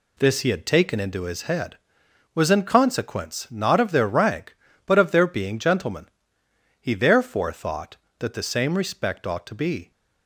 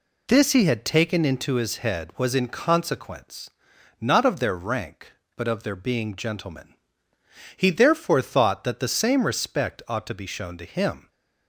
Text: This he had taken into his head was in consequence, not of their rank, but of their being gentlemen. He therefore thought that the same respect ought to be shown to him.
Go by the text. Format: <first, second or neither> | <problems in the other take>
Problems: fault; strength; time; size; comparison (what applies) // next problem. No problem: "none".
second | stops before "shown to him"; at 9.9 s